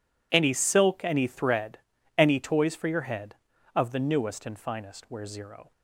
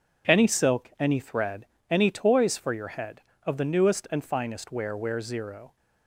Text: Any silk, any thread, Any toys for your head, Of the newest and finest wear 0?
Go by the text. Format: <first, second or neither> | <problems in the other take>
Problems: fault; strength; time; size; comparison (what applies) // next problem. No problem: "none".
first | says "wear" twice; at 4.9 s